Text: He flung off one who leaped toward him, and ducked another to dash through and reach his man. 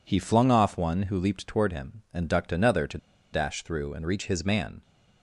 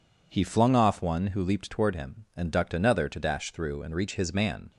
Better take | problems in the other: second | pauses between "to" and "dash"; slight; at 2.9 s; 0.35 s long

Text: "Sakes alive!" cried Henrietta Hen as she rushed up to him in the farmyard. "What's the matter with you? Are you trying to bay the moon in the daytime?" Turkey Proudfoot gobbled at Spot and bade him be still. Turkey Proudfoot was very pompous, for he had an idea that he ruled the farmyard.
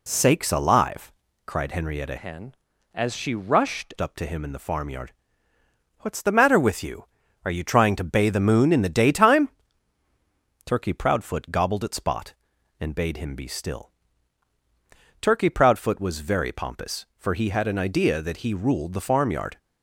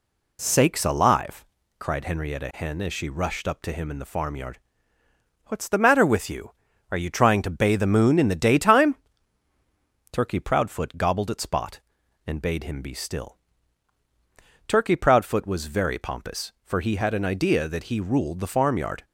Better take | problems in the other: second | changes voice from "Hen" to "rushed"; from 2.1 to 3.9 s; 1.8 s long

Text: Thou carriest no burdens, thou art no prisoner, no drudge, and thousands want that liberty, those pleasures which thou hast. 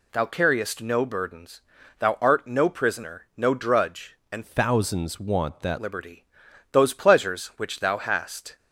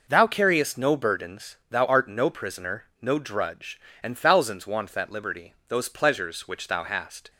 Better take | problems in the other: second | changes voice from "thousands" to "that"; from 4.4 to 5.7 s; 1.3 s long

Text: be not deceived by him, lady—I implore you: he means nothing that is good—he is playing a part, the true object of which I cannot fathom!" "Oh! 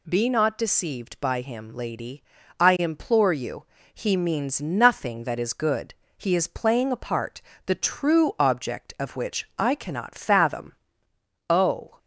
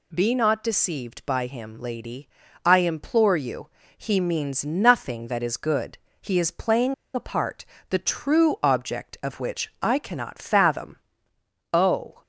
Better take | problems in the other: first | pauses between "playing" and "a"; slight; at 6.9 s; 0.21 s long

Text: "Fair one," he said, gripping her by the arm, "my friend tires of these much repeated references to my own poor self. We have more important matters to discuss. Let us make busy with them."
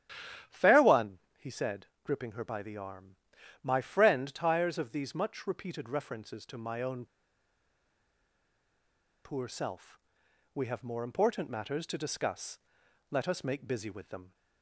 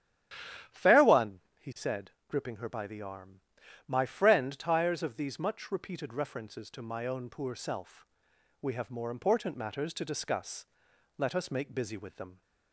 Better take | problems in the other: second | starts louder than the rest; strong; until 1.6 s; 11 dB; strong in the second // pauses between "own" and "poor"; strong; at 7.0 s; 2.2 s long

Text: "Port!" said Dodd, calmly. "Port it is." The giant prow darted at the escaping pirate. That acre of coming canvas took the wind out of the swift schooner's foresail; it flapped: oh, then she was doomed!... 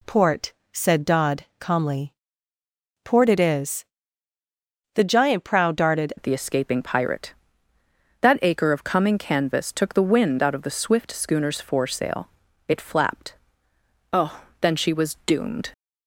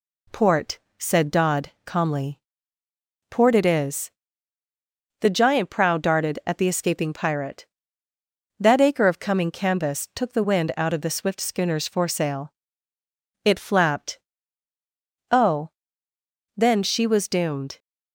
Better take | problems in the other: second | changes voice at "at"; from 6.1 s on; 9.6 s long

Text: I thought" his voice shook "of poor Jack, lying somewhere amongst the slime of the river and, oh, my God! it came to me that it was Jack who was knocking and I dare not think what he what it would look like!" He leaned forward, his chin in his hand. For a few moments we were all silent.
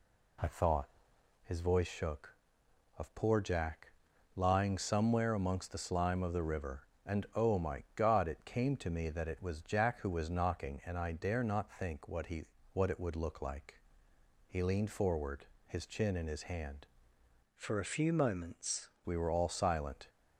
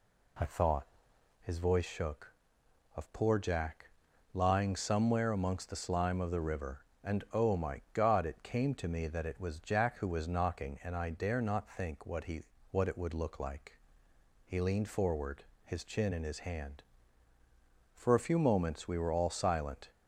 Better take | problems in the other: second | pauses between "thought" and "his"; noticeable; at 0.8 s; 0.56 s long; noticeable in the second // pauses between "he" and "what"; slight; at 12.4 s; 0.28 s long; slight in the second // changes voice from "For" to "moments"; from 17.5 to 18.8 s; 1.3 s long

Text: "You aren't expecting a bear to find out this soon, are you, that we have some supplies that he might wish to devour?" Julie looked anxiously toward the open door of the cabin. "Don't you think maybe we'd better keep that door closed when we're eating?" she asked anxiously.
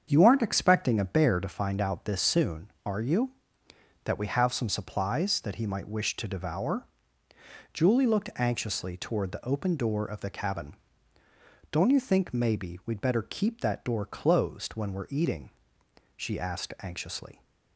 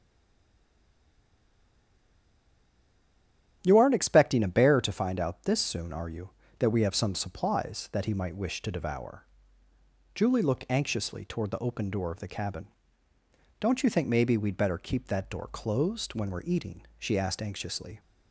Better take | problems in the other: first | stays silent before the first word; strong; until 3.6 s; 3.6 s long // starts louder than the rest; strong; until 4.6 s; 10 dB; strong in the first

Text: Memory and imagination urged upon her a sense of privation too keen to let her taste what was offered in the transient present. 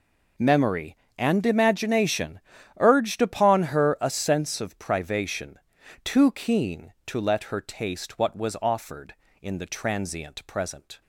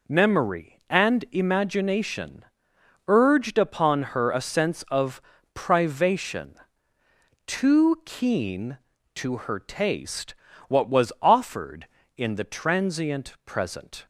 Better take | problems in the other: first | pauses between "imagination" and "urged"; noticeable; at 2.4 s; 0.62 s long; also in the first // pauses between "of" and "privation"; slight; at 5.1 s; 0.36 s long // pauses between "privation" and "too"; noticeable; at 6.5 s; 0.94 s long; also in the first // skips "let"; at 9.3 s // pauses between "taste" and "what"; slight; at 10.3 s; 0.32 s long

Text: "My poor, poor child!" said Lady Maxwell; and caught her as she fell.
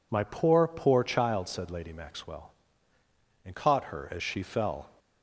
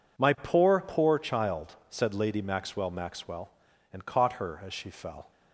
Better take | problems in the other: first | says "Maxwell" twice; at 2.9 s

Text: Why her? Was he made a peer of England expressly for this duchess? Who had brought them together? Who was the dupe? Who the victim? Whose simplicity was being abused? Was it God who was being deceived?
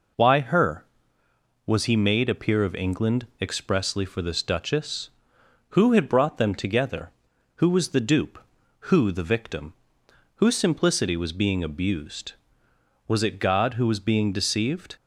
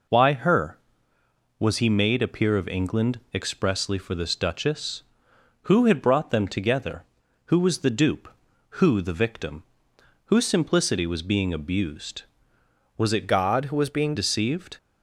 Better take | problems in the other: first | changes voice from "God" to "being"; from 13.2 to 14.1 s; 0.9 s long

